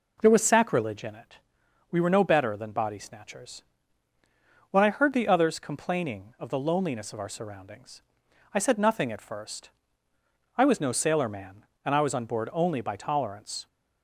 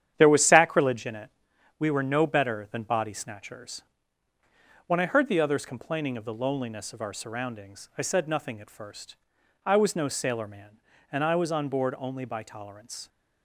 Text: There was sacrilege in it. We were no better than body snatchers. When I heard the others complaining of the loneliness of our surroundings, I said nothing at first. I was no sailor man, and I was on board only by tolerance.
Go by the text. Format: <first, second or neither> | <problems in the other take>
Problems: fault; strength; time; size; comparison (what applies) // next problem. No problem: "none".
first | gets quieter; strong; throughout; 7.5 dB